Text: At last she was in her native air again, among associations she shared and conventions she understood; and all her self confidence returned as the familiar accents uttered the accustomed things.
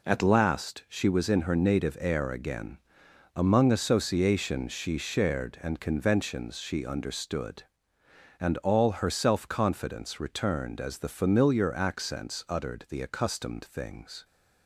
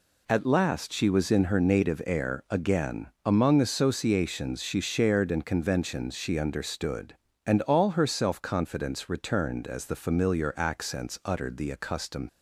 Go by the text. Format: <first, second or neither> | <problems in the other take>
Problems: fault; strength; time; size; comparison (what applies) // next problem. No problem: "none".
first | stops before "things"; at 12.2 s